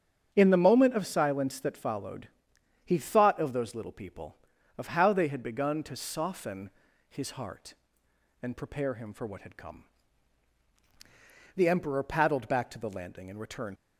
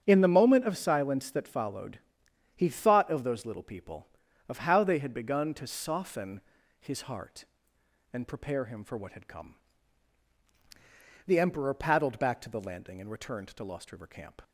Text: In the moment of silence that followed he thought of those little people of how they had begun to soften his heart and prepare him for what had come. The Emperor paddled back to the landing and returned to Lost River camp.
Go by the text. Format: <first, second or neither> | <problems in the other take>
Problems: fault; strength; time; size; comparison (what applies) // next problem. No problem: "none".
second | starts louder than the rest; strong; until 1.3 s; 8.5 dB; strong in the second // pauses between "followed" and "he"; noticeable; at 2.2 s; 0.56 s long; noticeable in the second // pauses between "soften" and "his"; at 6.7 s; 0.38 s long; also in the second // stops before "to Lost River camp"; at 13.7 s